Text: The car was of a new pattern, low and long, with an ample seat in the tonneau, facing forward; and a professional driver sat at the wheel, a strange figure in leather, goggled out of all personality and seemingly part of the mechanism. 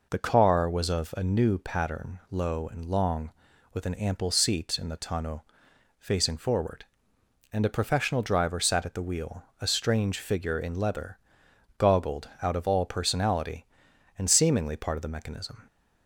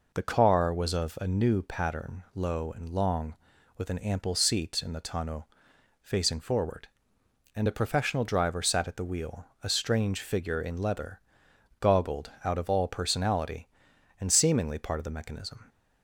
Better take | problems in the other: neither | none

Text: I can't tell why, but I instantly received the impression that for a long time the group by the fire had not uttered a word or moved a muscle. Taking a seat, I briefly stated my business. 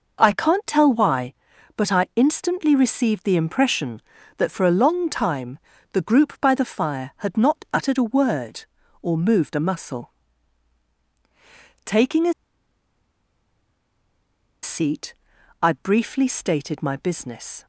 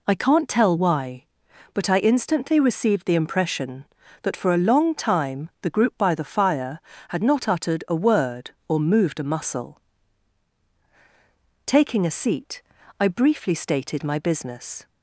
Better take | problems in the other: second | pauses between "time" and "the"; slight; at 5.5 s; 0.34 s long // pauses between "a" and "seat"; strong; at 12.3 s; 2.3 s long

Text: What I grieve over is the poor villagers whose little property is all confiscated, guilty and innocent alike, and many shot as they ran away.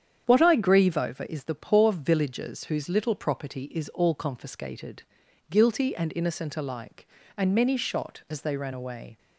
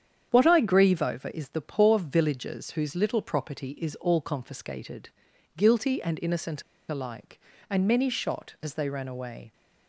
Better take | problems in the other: first | starts louder than the rest; strong; until 1.3 s; 8.5 dB; strong in the first // pauses between "innocent" and "alike"; slight; at 6.6 s; 0.26 s long

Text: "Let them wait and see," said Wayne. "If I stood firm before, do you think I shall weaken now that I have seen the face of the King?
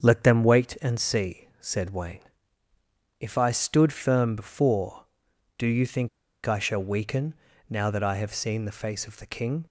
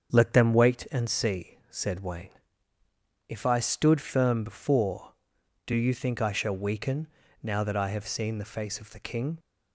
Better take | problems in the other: second | starts louder than the rest; strong; until 1.0 s; 7.5 dB; strong in the second // pauses between "think" and "I"; at 6.0 s; 0.36 s long // pauses between "weaken" and "now"; slight; at 7.3 s; 0.34 s long; slight in the second

